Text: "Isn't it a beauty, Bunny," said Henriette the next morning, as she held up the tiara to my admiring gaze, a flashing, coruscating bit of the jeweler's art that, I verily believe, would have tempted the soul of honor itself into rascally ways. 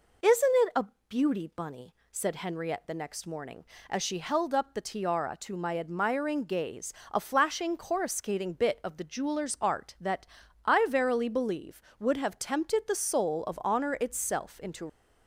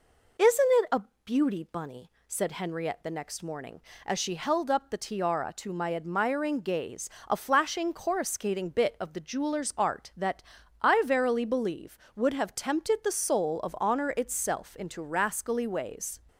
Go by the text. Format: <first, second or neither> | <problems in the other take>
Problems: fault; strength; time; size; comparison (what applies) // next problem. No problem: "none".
second | pauses between "a" and "beauty"; slight; at 0.8 s; 0.22 s long; slight in the second // stops before "rascally ways"; at 14.8 s